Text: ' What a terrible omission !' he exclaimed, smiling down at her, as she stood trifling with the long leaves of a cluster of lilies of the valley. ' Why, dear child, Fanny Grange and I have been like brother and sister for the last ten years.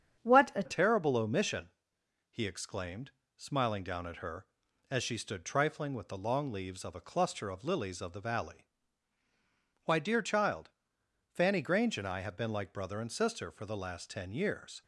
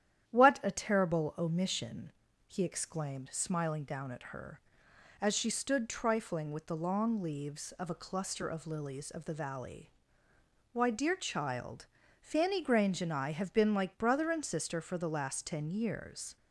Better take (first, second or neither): second